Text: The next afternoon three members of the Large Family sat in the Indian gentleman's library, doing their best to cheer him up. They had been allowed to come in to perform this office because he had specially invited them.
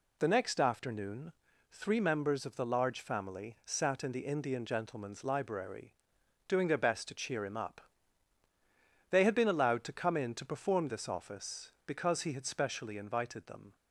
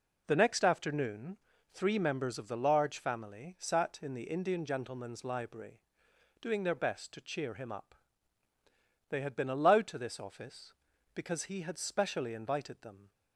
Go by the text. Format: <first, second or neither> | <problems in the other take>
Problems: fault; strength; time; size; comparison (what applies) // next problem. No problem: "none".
first | pauses between "afternoon" and "three"; slight; at 1.3 s; 0.34 s long; also in the first // skips "come in to perform"; at 9.9 s